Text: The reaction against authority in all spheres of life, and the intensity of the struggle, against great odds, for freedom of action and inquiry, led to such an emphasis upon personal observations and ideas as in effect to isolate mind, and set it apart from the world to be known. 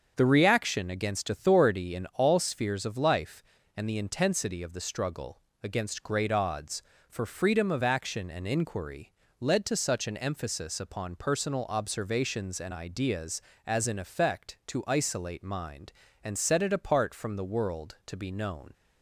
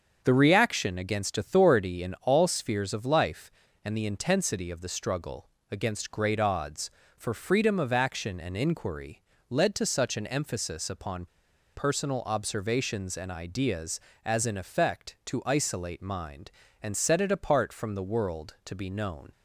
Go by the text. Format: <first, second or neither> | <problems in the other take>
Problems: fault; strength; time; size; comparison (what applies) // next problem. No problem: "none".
first | starts louder than the rest; until 1.2 s; 7 dB; also in the first // pauses between "upon" and "personal"; noticeable; at 11.2 s; 0.49 s long